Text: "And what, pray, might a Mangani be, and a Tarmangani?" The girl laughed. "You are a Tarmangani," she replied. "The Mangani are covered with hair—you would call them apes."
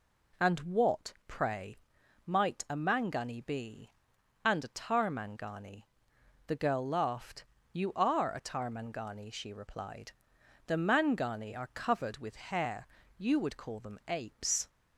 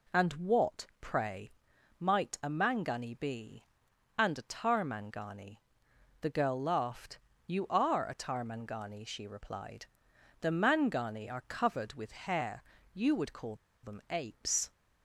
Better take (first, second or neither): first